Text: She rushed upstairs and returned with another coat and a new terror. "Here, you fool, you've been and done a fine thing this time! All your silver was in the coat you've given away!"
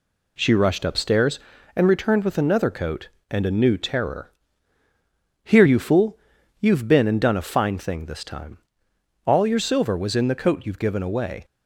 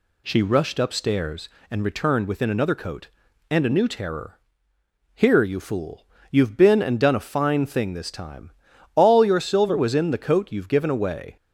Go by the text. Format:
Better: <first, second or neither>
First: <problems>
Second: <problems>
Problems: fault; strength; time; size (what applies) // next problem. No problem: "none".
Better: first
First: none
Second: says "within" for "with"; at 2.2 s